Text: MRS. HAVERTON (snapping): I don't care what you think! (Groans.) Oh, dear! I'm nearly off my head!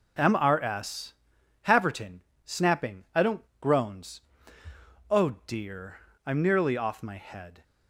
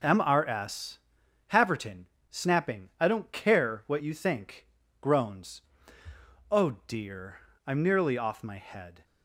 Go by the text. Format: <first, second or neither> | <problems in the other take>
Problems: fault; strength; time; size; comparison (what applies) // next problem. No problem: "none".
second | starts louder than the rest; until 1.7 s; 6.5 dB; also in the second // skips "care what you think"; at 3.5 s